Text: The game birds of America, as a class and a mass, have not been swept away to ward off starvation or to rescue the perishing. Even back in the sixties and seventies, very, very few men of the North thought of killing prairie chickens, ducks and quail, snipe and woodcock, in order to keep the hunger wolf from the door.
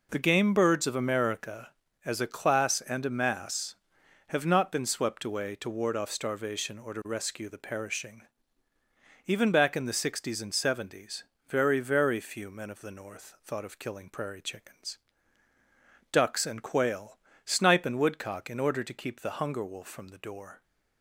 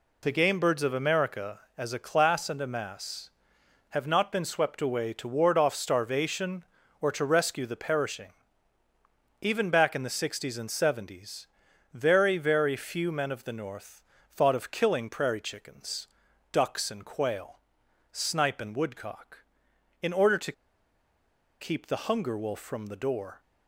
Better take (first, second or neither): first